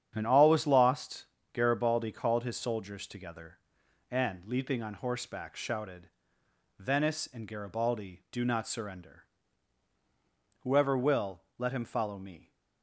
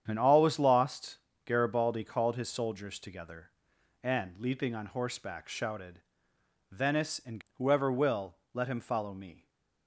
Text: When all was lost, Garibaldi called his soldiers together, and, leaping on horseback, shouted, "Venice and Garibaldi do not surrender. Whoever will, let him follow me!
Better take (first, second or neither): first